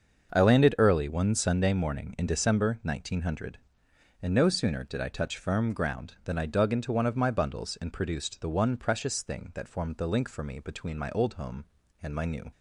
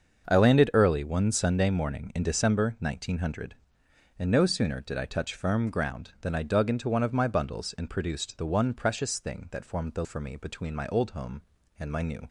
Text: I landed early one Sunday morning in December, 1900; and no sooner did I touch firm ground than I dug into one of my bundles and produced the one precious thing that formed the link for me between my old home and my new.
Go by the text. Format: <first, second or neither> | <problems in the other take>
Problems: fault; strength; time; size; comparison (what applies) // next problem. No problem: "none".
first | starts louder than the rest; until 1.3 s; 6.5 dB; also in the first // skips "link"; at 10.0 s